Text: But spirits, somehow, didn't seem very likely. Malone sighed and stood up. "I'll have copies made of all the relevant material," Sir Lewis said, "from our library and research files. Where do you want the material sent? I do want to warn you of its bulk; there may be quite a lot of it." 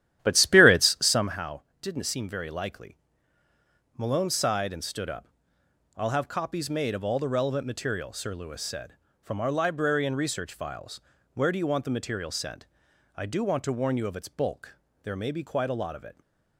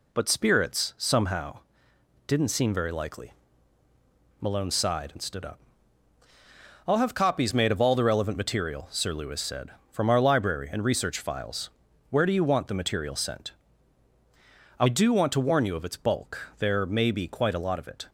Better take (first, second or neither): second